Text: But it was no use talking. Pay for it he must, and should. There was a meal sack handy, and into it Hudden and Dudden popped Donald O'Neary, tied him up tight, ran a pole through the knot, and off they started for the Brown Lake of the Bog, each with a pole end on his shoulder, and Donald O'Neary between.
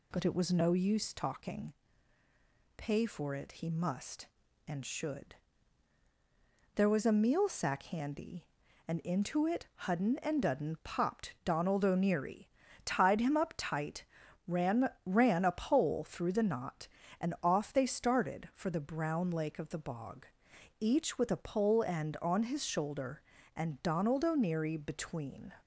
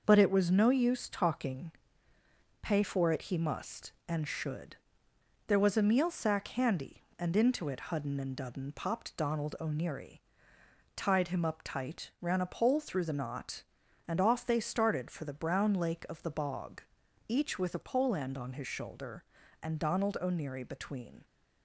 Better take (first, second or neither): second